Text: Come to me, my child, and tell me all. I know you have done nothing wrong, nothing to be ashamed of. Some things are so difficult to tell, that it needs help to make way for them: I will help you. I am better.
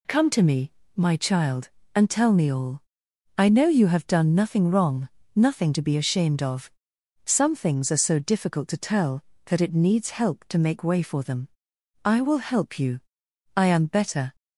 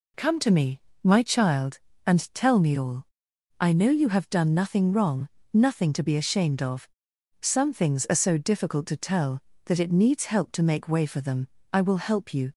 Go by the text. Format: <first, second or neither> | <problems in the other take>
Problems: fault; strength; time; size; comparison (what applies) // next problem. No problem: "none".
first | stops before "I am better"; at 12.5 s